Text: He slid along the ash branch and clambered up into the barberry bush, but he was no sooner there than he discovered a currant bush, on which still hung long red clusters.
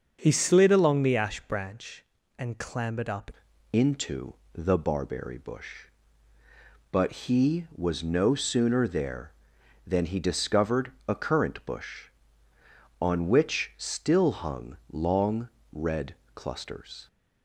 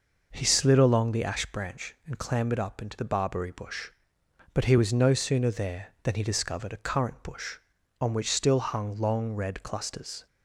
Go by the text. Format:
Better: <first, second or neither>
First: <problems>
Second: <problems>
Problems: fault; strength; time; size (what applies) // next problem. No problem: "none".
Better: second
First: starts louder than the rest; until 1.2 s; 6.5 dB // changes voice at "into"; from 3.7 s on; 13.3 s long // pauses between "into" and "the"; slight; at 4.3 s; 0.18 s long // pauses between "discovered" and "a"; slight; at 10.9 s; 0.16 s long // pauses between "long" and "red"; slight; at 15.4 s; 0.24 s long // pauses between "red" and "clusters"; slight; at 16.1 s; 0.22 s long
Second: none